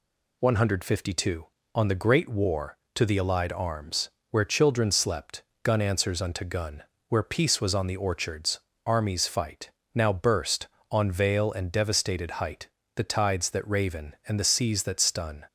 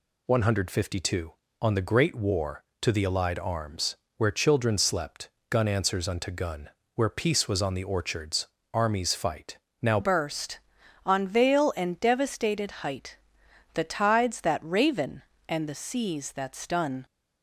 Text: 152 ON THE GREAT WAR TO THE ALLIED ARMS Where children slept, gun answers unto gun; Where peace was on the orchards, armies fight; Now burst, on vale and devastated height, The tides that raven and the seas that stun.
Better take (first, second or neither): first